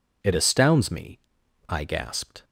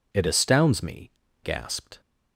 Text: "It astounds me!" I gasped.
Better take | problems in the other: first | skips "I"; at 1.2 s

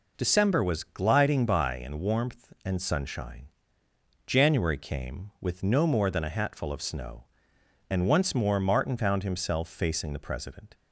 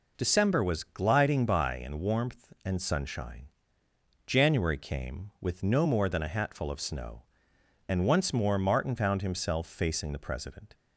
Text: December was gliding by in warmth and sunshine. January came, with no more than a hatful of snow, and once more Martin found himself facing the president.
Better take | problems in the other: neither | none

